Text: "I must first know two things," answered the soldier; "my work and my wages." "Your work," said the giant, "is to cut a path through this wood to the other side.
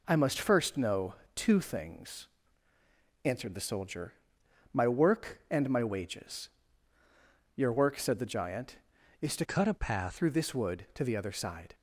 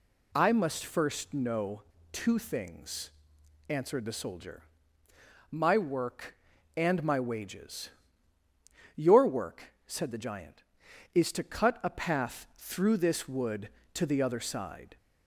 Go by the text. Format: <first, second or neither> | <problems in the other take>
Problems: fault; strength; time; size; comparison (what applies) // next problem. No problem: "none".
second | pauses between "know" and "two"; slight; at 1.1 s; 0.22 s long; slight in the second // changes voice from "cut" to "path"; from 9.4 to 10.1 s; 0.7 s long